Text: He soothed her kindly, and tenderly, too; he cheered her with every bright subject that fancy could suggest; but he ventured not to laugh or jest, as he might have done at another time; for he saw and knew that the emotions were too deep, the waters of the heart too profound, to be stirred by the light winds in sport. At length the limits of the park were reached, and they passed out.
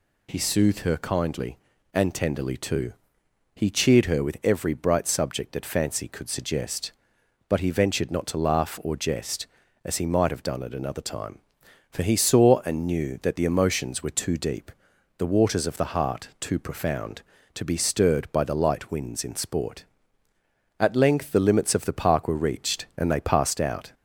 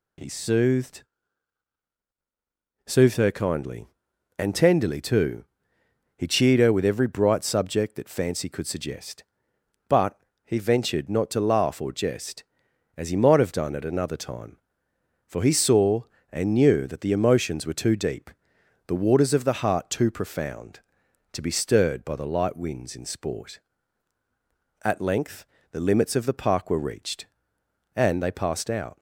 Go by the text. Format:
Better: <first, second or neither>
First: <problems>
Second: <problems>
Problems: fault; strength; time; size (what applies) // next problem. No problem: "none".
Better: first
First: none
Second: says "soothed" twice; at 2.8 s // pauses between "but" and "he"; slight; at 10.1 s; 0.26 s long // pauses between "length" and "the"; slight; at 25.4 s; 0.26 s long